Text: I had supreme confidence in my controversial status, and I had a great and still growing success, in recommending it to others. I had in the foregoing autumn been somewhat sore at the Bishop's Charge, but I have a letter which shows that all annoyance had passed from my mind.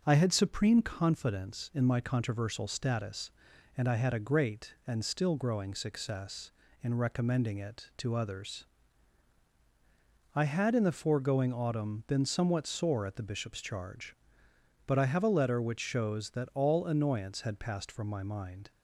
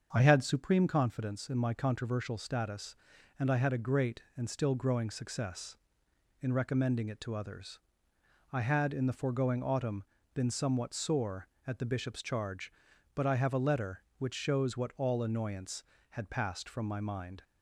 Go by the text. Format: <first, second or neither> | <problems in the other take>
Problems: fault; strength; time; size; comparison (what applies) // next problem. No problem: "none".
first | starts louder than the rest; until 1.1 s; 7 dB // pauses between "autumn" and "been"; slight; at 10.0 s; 0.30 s long // says "what" for "that"; at 14.7 s